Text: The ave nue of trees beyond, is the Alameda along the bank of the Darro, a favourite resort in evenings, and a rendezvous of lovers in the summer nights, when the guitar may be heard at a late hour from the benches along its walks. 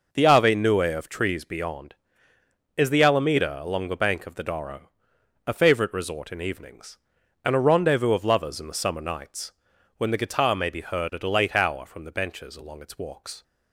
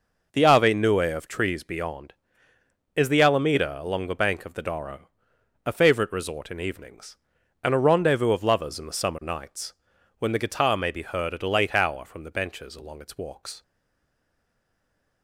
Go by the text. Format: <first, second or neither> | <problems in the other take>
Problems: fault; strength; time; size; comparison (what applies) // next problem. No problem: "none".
first | stays silent after the last word; noticeable; from 13.6 s on; 1.6 s long